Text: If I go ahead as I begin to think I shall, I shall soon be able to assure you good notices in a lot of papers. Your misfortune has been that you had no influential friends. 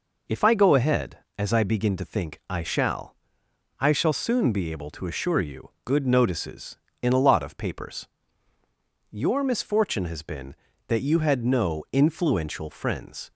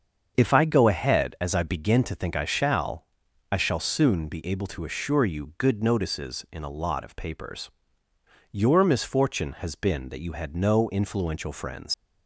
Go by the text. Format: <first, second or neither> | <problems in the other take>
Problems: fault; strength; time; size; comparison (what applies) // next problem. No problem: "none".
first | starts louder than the rest; until 1.3 s; 7 dB // leaves "friends" unfinished; at 11.9 s; 90 ms